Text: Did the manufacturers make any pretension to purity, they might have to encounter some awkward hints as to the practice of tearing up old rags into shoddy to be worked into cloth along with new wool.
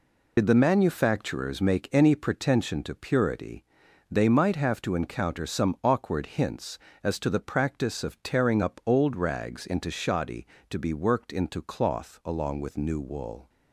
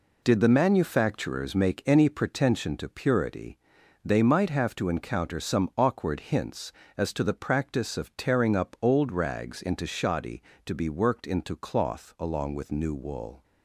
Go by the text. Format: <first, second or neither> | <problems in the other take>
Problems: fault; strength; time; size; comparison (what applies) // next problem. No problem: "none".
second | loses the start of "Did"; at 0.3 s; 65 ms